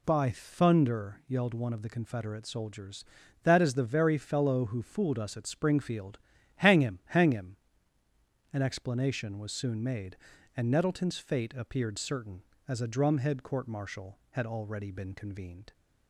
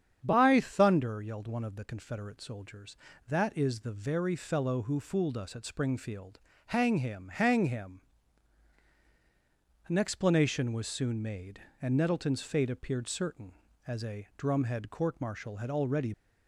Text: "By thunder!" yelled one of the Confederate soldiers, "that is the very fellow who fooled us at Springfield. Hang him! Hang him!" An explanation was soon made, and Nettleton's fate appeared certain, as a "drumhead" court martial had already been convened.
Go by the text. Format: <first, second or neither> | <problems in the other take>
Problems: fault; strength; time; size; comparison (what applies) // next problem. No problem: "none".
first | starts louder than the rest; strong; until 1.2 s; 8 dB // stops before "been convened"; at 16.1 s